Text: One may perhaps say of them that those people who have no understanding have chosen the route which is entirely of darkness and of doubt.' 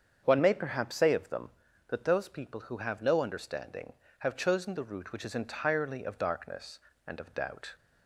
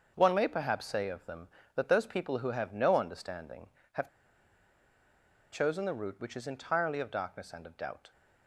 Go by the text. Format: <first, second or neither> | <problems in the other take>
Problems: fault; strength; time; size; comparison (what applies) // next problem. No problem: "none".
first | starts louder than the rest; until 1.1 s; 6.5 dB; strong in the first // pauses between "have" and "chosen"; strong; at 4.0 s; 1.4 s long